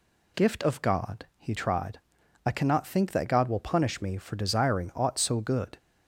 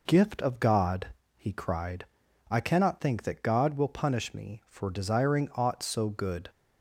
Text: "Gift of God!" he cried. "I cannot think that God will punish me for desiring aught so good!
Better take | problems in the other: second | says "tried" for "cried"; at 1.5 s

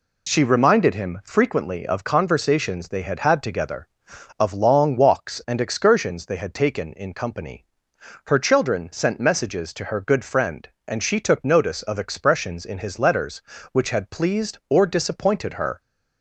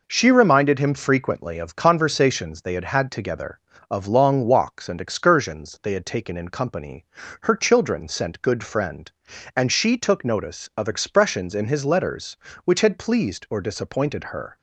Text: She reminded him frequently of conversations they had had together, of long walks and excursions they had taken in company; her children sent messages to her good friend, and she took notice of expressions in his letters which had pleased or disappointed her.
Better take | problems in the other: first | skips "messages to her"; at 8.4 s

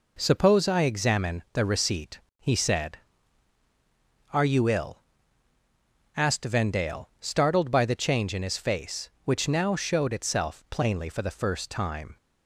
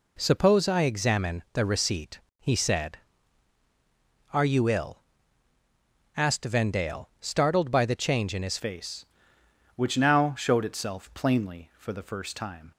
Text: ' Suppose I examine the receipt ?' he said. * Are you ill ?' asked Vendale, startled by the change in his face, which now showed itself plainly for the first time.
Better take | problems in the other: first | changes voice at "face"; from 8.5 s on; 4.2 s long

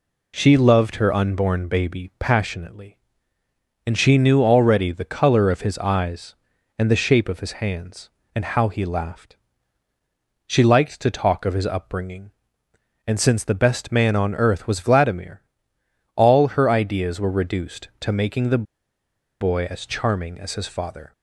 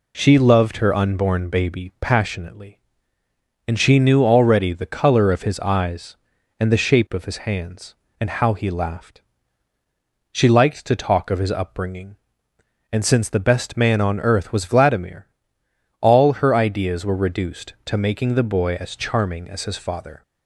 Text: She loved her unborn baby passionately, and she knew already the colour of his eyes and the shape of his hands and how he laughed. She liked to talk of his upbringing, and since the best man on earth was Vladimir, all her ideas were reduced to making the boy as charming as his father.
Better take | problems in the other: second | pauses between "the" and "boy"; noticeable; at 18.6 s; 0.76 s long

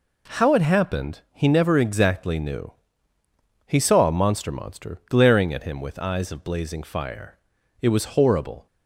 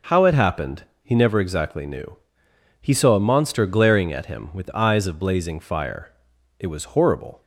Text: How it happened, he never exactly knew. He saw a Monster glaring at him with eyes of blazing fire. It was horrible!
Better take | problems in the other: second | says "Monster" twice; at 4.5 s

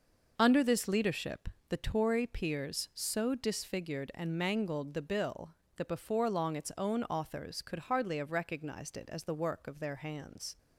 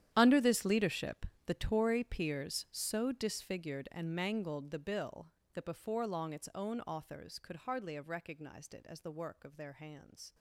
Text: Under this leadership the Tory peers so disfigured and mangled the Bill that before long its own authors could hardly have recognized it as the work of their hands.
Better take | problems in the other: first | gets quieter; strong; throughout; 18 dB // pauses between "leadership" and "the"; slight; at 1.2 s; 0.22 s long; slight in the first

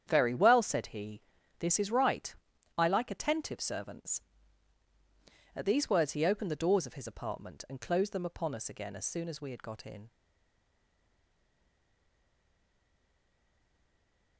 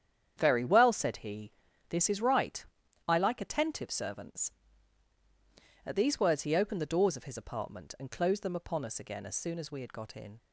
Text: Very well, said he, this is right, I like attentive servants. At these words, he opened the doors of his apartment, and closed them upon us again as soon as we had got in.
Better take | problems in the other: second | starts louder than the rest; strong; until 1.0 s; 9 dB; strong in the second // stays silent after the last word; strong; from 10.0 s on; 4.3 s long

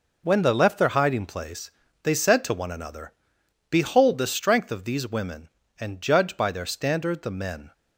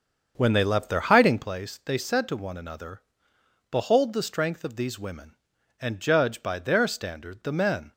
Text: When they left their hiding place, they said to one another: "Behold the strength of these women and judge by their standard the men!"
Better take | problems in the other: first | starts louder than the rest; until 1.5 s; 6.5 dB

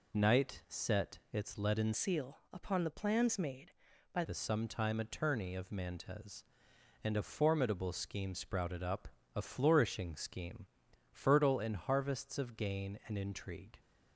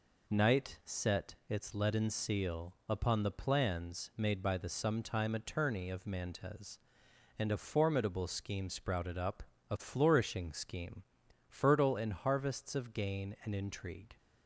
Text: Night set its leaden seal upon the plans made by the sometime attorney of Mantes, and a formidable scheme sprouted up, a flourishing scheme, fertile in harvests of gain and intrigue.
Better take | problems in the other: second | changes voice from "seal" to "by"; from 1.9 to 4.2 s; 2.3 s long

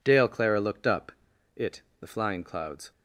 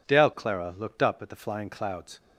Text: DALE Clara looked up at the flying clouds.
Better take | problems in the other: second | says "it" for "at"; at 1.5 s

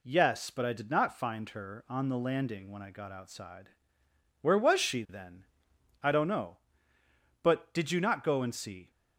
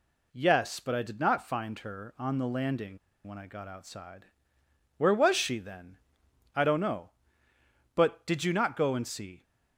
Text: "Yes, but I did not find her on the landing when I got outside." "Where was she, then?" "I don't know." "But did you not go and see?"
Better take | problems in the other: first | pauses between "landing" and "when"; slight; at 2.9 s; 0.28 s long

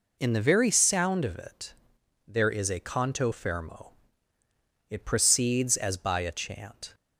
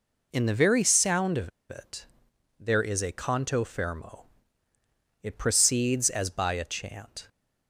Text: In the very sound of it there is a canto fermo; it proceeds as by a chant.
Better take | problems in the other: first | pauses between "of" and "it"; slight; at 1.5 s; 0.20 s long // pauses between "it" and "there"; noticeable; at 2.0 s; 0.52 s long; noticeable in the first

